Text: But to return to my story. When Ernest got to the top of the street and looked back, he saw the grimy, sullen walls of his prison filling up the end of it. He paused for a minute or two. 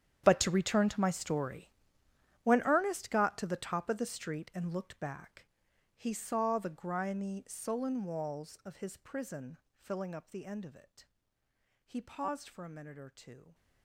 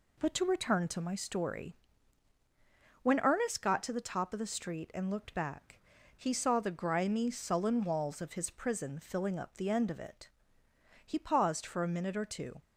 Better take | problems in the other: second | gets quieter; strong; throughout; 18.5 dB // pauses between "prison" and "filling"; slight; at 9.5 s; 0.18 s long

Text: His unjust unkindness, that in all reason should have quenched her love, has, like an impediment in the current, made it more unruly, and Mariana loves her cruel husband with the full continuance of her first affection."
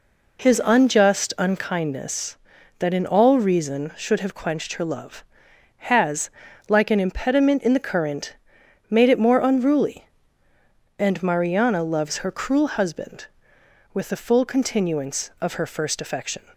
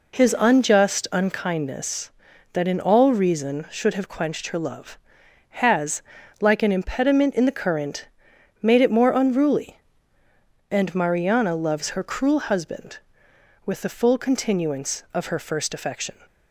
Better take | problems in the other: neither | none

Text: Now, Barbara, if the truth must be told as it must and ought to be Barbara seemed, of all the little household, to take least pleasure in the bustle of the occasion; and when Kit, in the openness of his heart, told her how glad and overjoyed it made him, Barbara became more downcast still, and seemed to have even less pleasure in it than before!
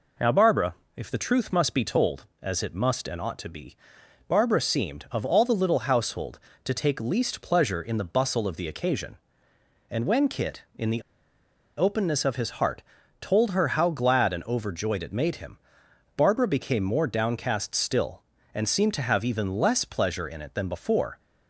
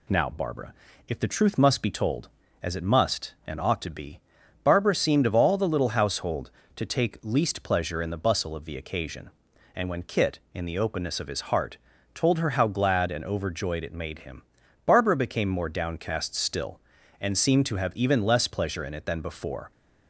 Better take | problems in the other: second | pauses between "be" and "Barbara"; noticeable; at 3.7 s; 0.50 s long; also in the second // pauses between "the" and "openness"; noticeable; at 11.0 s; 0.75 s long

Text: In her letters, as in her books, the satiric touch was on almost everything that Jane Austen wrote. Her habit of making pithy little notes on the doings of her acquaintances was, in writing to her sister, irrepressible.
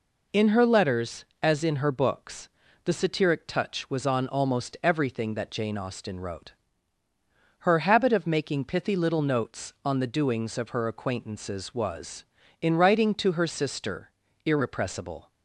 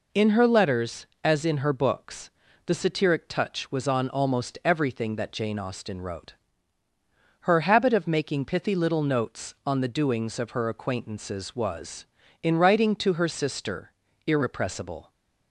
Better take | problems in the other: neither | none

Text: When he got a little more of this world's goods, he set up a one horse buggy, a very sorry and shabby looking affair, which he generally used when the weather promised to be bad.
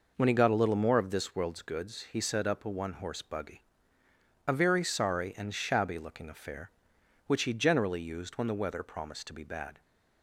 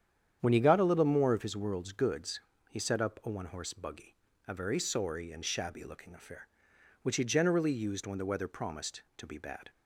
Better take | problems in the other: first | starts louder than the rest; strong; until 1.4 s; 9 dB // says "his" for "this"; at 1.4 s

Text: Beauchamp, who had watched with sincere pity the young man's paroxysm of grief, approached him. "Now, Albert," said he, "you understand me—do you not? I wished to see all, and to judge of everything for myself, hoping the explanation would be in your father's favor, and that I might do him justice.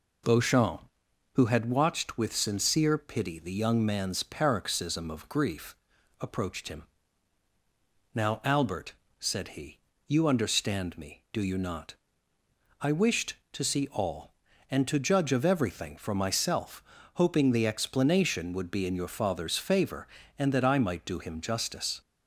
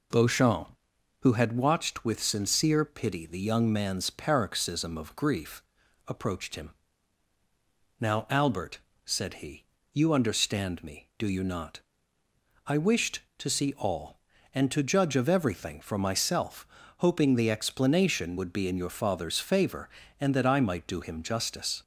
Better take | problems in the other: neither | none

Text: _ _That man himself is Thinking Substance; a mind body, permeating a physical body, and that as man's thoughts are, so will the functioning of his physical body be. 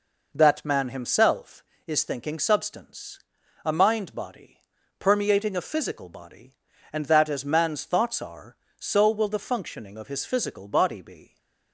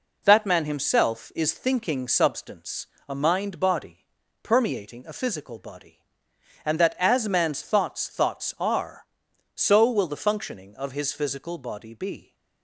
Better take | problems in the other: first | says "thoughts" twice; at 8.0 s

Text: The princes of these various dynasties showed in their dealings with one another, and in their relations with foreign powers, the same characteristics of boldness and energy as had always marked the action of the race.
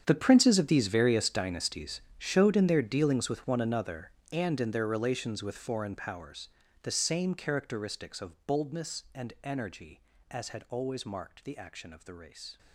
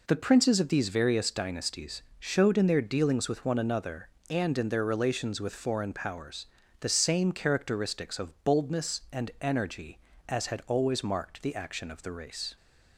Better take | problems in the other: second | gets quieter; strong; throughout; 18 dB // pauses between "dynasties" and "showed"; slight; at 2.0 s; 0.16 s long; slight in the second

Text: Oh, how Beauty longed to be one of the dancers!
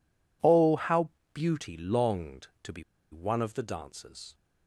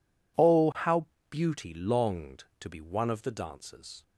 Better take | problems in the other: second | pauses between "how" and "Beauty"; slight; at 1.0 s; 0.24 s long; slight in the second // pauses between "be" and "one"; slight; at 2.8 s; 0.29 s long

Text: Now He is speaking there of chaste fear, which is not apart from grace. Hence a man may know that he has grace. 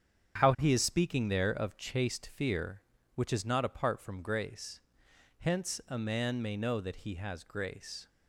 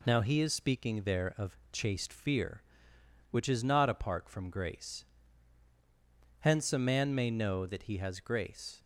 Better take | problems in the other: second | starts louder than the rest; strong; until 1.4 s; 8 dB // says "How" for "Now"; at 0.4 s

